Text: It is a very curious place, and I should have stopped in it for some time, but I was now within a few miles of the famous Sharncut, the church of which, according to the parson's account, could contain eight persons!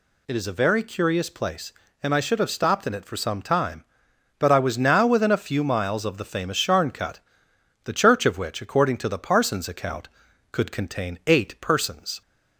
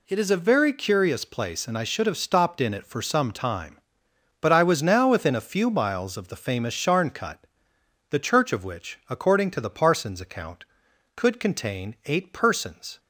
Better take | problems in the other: neither | none

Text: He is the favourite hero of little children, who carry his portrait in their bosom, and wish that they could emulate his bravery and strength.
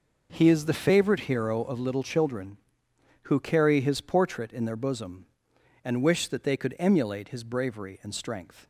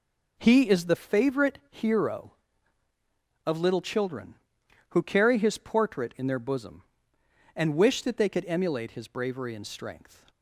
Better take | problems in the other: neither | none

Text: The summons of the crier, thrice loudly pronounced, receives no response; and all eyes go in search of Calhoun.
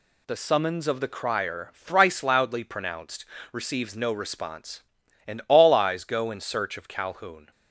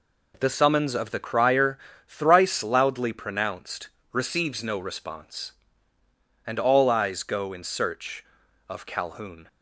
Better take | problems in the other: neither | none

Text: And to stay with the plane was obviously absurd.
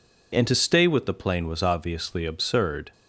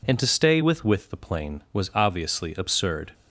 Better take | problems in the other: first | says "with" twice; at 0.8 s

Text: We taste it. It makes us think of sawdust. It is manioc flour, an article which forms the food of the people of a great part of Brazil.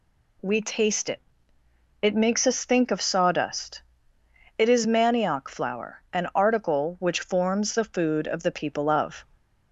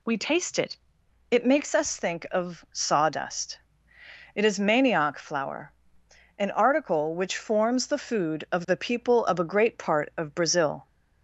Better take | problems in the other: second | stops before "a great part of Brazil"; at 9.3 s

